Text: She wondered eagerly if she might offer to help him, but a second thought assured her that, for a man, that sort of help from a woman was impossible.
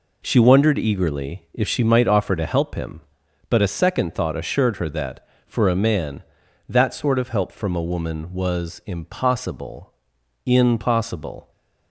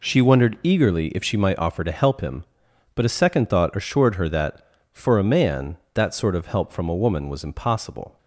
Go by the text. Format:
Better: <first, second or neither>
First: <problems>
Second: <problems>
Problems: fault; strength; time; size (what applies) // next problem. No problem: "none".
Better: second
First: says "impossible" twice; at 10.4 s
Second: none